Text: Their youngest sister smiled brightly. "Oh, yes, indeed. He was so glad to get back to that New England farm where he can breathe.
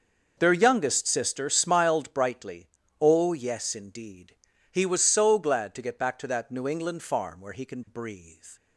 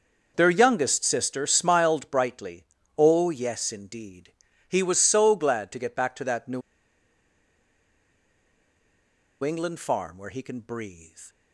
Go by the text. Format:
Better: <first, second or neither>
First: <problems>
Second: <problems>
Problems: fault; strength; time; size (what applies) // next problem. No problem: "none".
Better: first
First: none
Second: pauses between "New" and "England"; strong; at 6.6 s; 2.8 s long